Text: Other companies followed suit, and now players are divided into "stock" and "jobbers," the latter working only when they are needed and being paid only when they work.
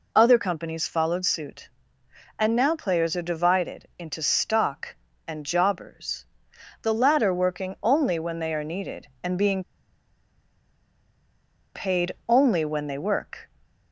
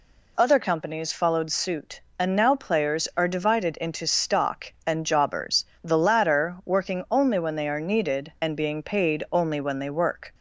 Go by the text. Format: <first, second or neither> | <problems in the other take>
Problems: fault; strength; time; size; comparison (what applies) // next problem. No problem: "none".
second | pauses between "being" and "paid"; strong; at 9.6 s; 2.1 s long // pauses between "paid" and "only"; slight; at 12.1 s; 0.16 s long